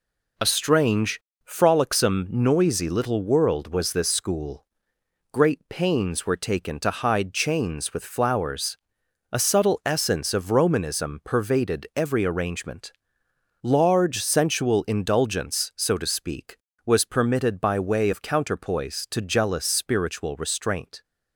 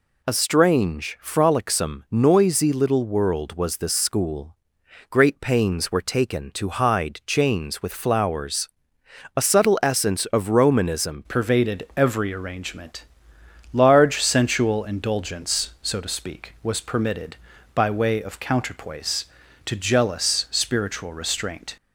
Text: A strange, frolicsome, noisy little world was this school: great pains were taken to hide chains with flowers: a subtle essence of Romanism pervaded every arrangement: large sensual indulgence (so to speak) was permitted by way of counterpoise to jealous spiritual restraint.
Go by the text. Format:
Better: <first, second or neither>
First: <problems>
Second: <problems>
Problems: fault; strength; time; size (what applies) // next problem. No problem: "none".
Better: first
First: none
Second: changes voice at "pervaded"; from 11.2 s on; 10.5 s long